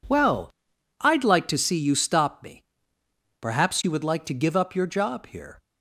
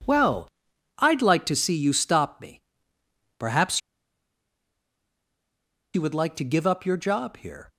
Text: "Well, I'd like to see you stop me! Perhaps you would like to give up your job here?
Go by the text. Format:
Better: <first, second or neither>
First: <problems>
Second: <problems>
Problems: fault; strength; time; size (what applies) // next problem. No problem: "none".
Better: first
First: none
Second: pauses between "Perhaps" and "you"; strong; at 3.7 s; 2.1 s long